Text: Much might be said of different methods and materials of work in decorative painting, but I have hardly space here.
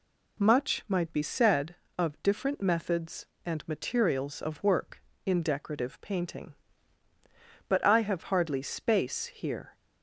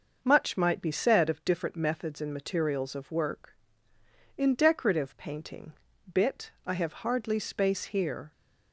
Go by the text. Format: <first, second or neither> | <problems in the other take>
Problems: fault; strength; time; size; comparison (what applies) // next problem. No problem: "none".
first | says "bit" for "but"; at 6.1 s